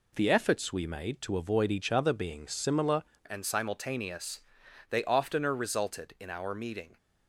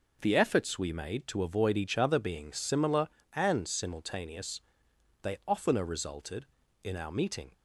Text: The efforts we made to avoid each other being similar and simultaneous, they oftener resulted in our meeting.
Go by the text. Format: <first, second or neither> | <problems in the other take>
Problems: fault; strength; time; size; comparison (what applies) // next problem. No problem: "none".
second | changes voice at "and"; from 3.2 s on; 3.7 s long